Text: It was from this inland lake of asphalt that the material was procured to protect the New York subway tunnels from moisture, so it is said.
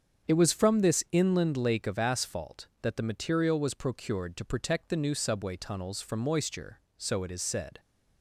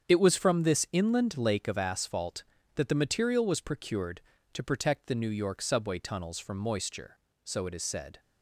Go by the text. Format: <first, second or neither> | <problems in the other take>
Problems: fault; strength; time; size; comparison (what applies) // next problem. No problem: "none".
second | starts louder than the rest; strong; until 1.3 s; 7.5 dB; strong in the second // skips "York"; at 5.1 s